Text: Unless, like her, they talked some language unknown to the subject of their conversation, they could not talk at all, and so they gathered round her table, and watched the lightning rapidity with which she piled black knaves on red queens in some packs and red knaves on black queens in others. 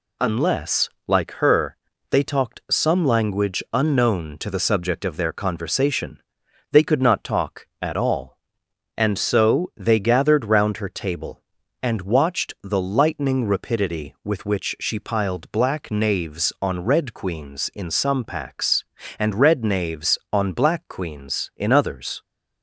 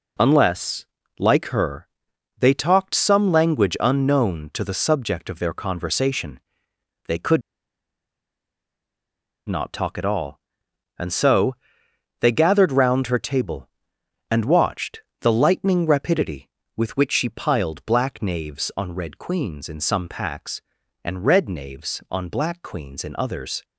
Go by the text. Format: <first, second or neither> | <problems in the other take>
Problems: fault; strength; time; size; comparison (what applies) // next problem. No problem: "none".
first | pauses between "could" and "not"; strong; at 7.4 s; 2.0 s long // pauses between "so" and "they"; noticeable; at 11.5 s; 0.64 s long // pauses between "watched" and "the"; slight; at 15.0 s; 0.20 s long